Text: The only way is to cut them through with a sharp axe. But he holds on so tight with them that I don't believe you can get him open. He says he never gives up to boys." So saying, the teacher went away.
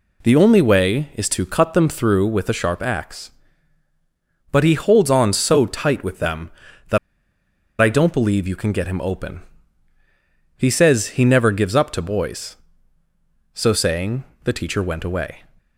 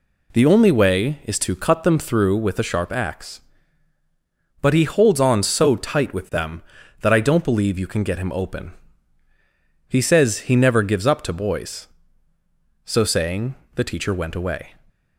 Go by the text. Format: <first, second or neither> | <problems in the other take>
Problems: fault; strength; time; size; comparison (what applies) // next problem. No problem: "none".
second | pauses between "that" and "I"; noticeable; at 6.9 s; 0.83 s long